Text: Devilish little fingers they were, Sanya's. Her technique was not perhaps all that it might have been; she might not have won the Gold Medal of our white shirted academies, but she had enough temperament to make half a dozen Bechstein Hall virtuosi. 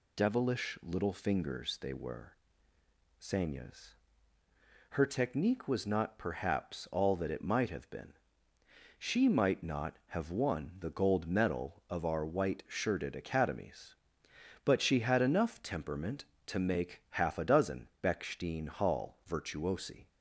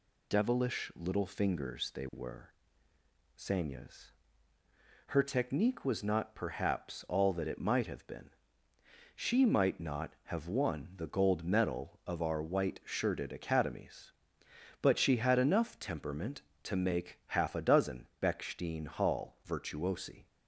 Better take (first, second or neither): neither